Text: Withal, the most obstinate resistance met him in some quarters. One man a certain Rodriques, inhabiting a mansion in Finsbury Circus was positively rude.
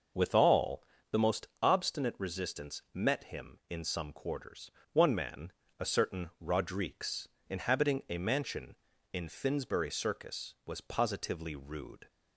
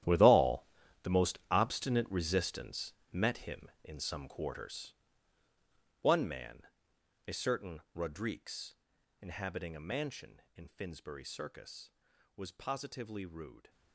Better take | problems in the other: first | gets quieter; strong; throughout; 15.5 dB // pauses between "resistance" and "met"; slight; at 2.9 s; 0.20 s long // pauses between "man" and "a"; noticeable; at 6.6 s; 0.62 s long; slight in the first

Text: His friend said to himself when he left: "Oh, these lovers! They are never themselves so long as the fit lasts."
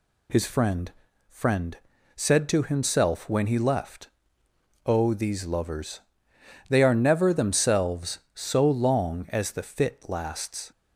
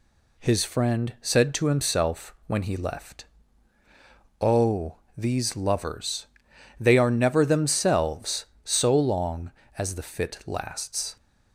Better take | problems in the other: second | says "friend" twice; at 1.2 s

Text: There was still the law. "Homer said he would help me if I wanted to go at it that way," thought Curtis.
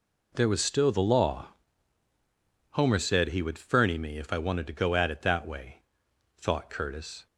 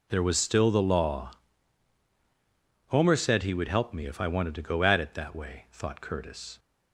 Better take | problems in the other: second | says "ferny" for "help"; at 3.5 s

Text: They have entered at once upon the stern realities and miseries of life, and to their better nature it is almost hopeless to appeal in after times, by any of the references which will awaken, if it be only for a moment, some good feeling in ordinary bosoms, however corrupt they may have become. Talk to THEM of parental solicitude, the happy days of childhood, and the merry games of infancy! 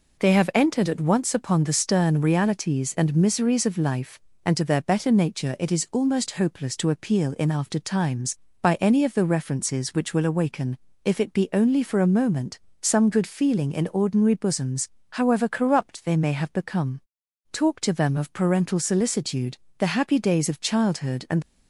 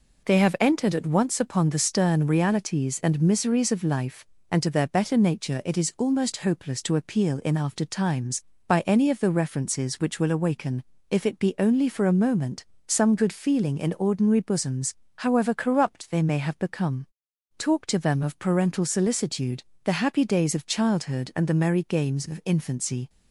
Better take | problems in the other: second | stops before "the merry games of infancy"; at 21.4 s

